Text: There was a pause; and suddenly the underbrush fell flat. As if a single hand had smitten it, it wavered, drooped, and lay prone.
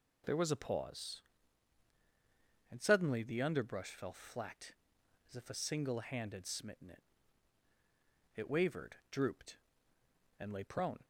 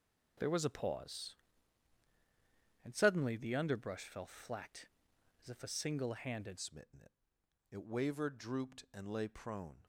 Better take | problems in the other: first | changes voice at "smitten"; from 6.5 s on; 3.3 s long

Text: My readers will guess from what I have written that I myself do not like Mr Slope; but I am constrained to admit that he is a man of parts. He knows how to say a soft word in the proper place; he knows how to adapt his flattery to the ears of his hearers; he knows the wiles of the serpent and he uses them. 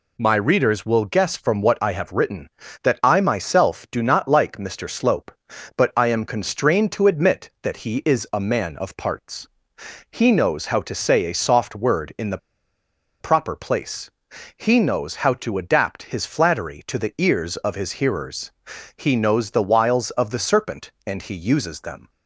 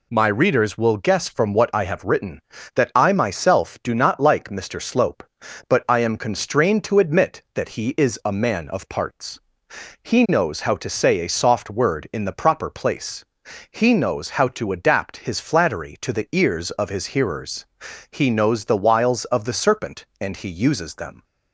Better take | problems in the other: second | pauses between "the" and "proper"; noticeable; at 12.3 s; 0.83 s long

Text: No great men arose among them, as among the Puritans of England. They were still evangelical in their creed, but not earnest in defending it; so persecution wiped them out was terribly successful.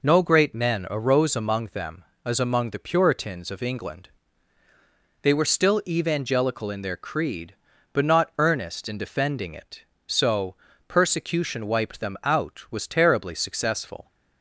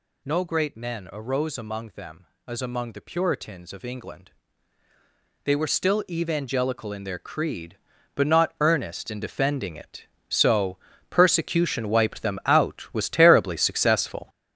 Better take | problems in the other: first | gets louder; strong; throughout; 8 dB // pauses between "so" and "persecution"; slight; at 10.7 s; 0.34 s long; slight in the first

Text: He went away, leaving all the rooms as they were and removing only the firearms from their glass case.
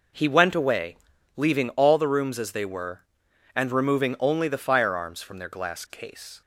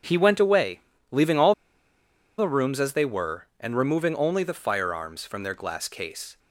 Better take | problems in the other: first | starts louder than the rest; strong; until 1.3 s; 7.5 dB // pauses between "all" and "the"; noticeable; at 1.5 s; 0.84 s long

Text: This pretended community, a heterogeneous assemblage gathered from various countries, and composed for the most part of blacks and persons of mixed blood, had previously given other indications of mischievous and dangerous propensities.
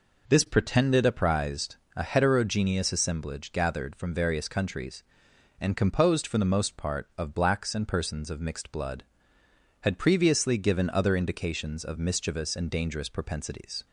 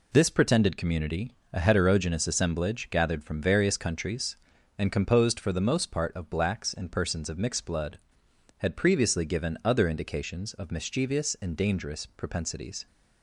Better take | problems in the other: second | says "apprised" for "community"; at 1.0 s

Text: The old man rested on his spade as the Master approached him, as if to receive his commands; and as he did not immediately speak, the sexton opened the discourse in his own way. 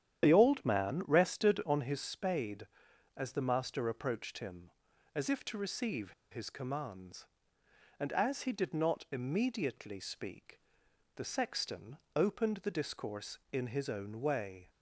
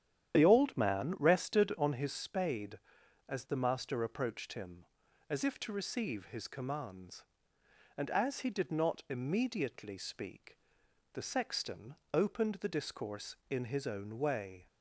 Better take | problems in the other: second | starts louder than the rest; strong; until 1.2 s; 10 dB; strong in the second // pauses between "receive" and "his"; slight; at 6.1 s; 0.19 s long // pauses between "sexton" and "opened"; slight; at 11.9 s; 0.18 s long; slight in the second

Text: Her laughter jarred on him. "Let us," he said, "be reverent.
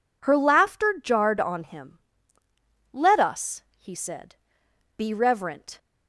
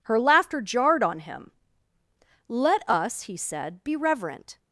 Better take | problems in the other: neither | none

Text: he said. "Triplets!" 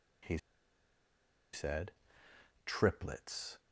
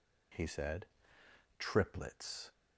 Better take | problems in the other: second | pauses between "he" and "said"; at 0.3 s; 1.1 s long

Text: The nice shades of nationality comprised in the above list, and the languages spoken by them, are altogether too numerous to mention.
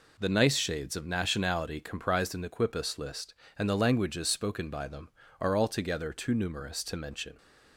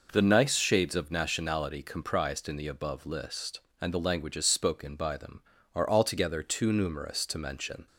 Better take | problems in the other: second | says "quipus" for "above"; at 2.4 s

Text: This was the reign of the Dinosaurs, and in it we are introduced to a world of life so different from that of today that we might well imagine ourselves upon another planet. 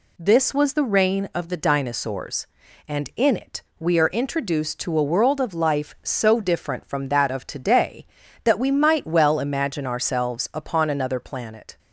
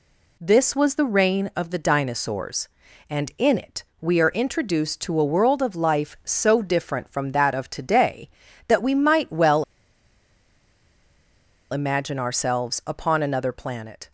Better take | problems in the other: first | pauses between "it" and "we"; slight; at 3.8 s; 0.18 s long; slight in the first // pauses between "well" and "imagine"; strong; at 9.6 s; 2.0 s long

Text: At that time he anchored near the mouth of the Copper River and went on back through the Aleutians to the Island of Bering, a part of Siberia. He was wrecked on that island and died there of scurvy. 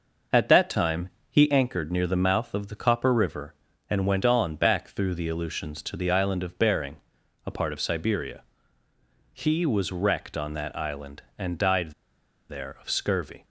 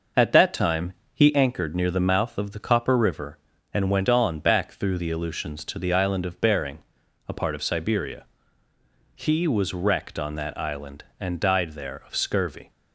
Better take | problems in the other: second | pauses between "time" and "he"; slight; at 1.0 s; 0.20 s long; slight in the second // pauses between "died" and "there"; noticeable; at 11.9 s; 0.58 s long

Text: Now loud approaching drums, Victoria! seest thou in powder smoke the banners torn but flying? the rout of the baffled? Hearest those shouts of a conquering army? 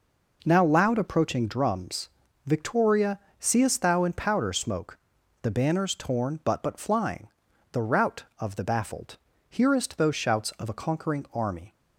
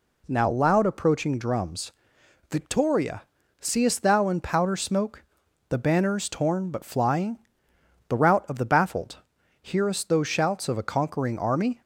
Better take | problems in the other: second | pauses between "smoke" and "the"; at 4.9 s; 0.42 s long; noticeable in the second // says "but" twice; at 6.6 s

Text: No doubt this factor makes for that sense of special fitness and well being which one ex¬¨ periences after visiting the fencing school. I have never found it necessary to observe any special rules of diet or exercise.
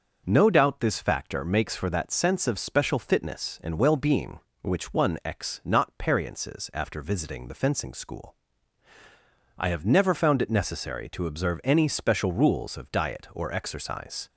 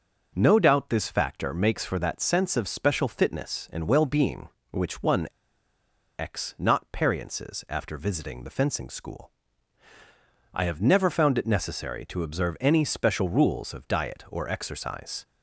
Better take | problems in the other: first | starts louder than the rest; until 1.3 s; 6 dB; also in the first // pauses between "one" and "ex"; noticeable; at 5.2 s; 0.90 s long

